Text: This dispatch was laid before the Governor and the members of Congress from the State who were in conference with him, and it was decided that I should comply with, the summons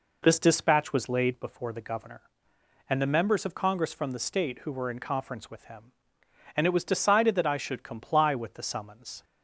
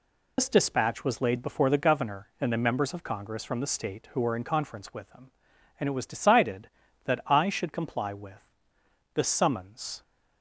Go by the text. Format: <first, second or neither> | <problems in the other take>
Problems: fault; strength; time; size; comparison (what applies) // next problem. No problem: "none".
first | loses the start of "This"; at 0.3 s; 105 ms